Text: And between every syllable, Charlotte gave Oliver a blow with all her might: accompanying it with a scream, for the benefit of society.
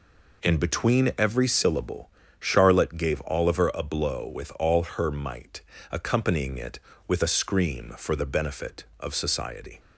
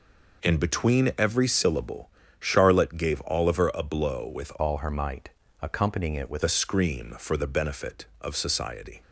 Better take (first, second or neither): first